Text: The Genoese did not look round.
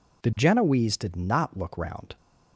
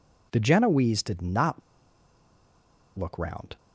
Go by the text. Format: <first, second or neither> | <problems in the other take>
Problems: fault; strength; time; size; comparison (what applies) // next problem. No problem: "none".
first | pauses between "not" and "look"; strong; at 1.6 s; 1.3 s long